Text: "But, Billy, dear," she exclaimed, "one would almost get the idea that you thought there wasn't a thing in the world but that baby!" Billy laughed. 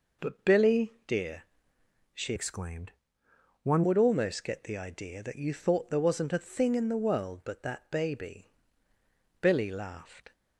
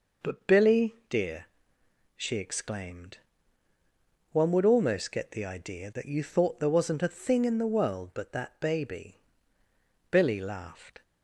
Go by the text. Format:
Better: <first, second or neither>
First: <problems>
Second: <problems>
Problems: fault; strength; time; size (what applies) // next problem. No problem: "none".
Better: second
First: changes voice from "exclaimed" to "one"; from 2.3 to 3.8 s; 1.5 s long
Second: none